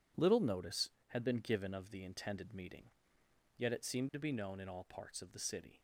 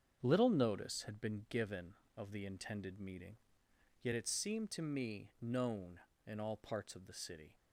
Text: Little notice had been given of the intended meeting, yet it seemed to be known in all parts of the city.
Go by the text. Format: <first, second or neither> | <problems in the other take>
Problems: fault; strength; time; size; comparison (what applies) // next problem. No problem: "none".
first | starts louder than the rest; strong; until 1.2 s; 7.5 dB // says "me" for "be"; at 4.8 s